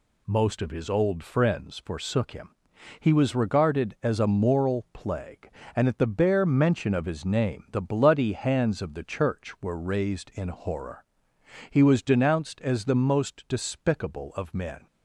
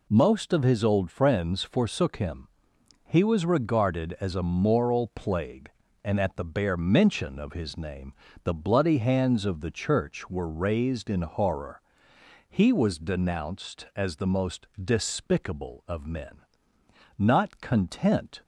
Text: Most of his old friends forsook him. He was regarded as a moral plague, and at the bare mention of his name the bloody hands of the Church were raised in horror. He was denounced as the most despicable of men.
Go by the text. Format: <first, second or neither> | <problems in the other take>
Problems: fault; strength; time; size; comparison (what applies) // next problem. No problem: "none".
first | pauses between "name" and "the"; slight; at 8.1 s; 0.32 s long // pauses between "most" and "despicable"; slight; at 14.6 s; 0.16 s long // goes on to say "Not content"; noticeable; from 17.1 s on; 1.2 s long